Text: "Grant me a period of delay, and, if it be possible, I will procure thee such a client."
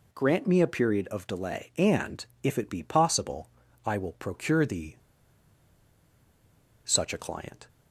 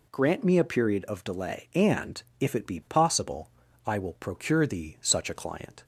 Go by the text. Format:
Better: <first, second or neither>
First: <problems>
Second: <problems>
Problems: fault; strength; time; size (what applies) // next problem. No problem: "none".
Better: second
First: pauses between "thee" and "such"; strong; at 4.9 s; 1.8 s long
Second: none